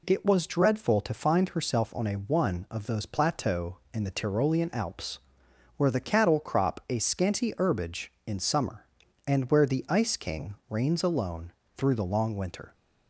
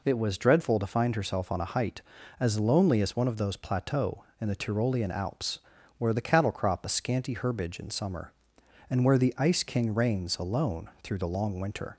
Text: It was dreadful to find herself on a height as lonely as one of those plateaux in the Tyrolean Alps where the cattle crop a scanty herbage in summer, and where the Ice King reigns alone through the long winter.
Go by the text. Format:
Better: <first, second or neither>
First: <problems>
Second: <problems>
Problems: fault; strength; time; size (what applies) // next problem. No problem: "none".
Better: second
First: skips "height as lonely as"; at 2.1 s // pauses between "Alps" and "where"; noticeable; at 5.1 s; 0.58 s long // pauses between "King" and "reigns"; slight; at 10.5 s; 0.16 s long // pauses between "alone" and "through"; slight; at 11.5 s; 0.26 s long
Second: pauses between "Alps" and "where"; at 5.5 s; 0.38 s long